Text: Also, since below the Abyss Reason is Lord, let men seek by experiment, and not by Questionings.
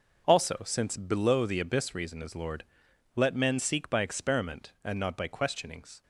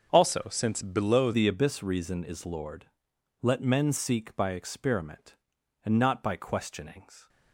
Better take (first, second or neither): first